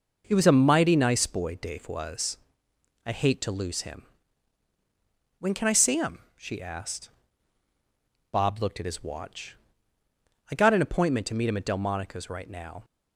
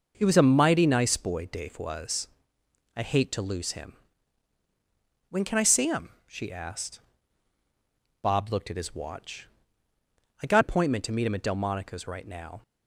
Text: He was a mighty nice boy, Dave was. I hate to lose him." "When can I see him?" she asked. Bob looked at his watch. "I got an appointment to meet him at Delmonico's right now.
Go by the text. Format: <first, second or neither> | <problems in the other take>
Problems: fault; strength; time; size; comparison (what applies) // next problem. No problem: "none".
first | skips "an"; at 10.6 s